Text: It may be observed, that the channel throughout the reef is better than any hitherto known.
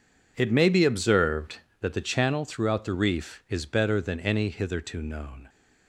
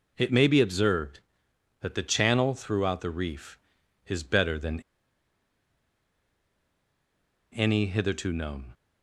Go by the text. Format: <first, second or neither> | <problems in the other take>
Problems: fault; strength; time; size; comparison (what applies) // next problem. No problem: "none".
first | pauses between "than" and "any"; strong; at 4.7 s; 2.7 s long